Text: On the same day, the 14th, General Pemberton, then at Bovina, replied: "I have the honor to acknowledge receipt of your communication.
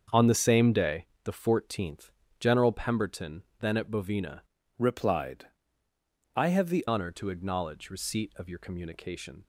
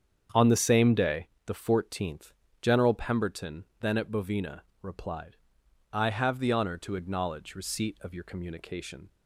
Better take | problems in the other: second | starts louder than the rest; until 1.3 s; 7 dB; strong in the second // changes voice from "replied" to "the"; from 4.7 to 6.8 s; 2.1 s long

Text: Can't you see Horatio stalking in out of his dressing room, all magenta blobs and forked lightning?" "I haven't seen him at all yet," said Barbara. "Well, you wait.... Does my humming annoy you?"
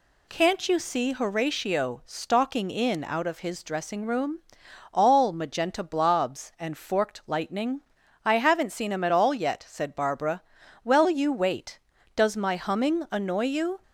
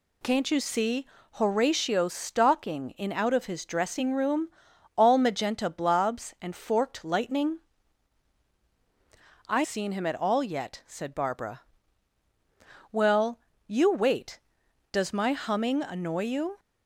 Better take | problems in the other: first | pauses between "see" and "Horatio"; slight; at 1.0 s; 0.28 s long // skips "haven't"; at 9.6 s

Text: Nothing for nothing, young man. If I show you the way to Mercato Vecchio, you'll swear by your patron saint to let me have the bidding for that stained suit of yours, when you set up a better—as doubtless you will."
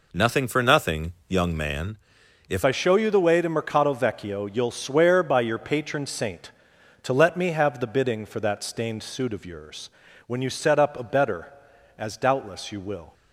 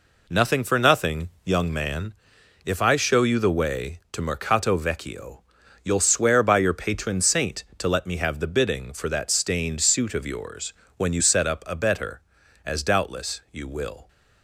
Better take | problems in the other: second | changes voice at "I"; from 2.6 s on; 10.5 s long

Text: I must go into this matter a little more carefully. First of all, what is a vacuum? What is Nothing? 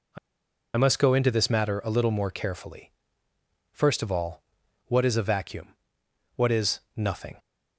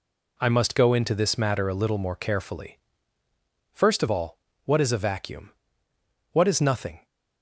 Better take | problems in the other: second | pauses between "I" and "must"; noticeable; at 0.1 s; 0.58 s long

